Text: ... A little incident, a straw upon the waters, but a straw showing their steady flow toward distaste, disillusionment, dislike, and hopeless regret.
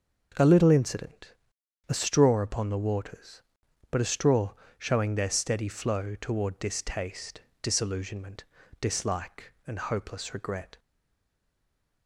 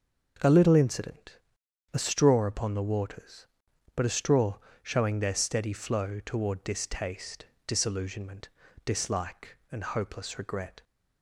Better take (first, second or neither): second